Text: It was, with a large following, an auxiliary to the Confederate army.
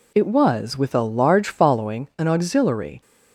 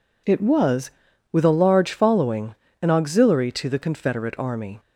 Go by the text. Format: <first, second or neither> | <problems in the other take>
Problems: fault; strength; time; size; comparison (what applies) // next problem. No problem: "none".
second | stops before "to the Confederate army"; at 3.0 s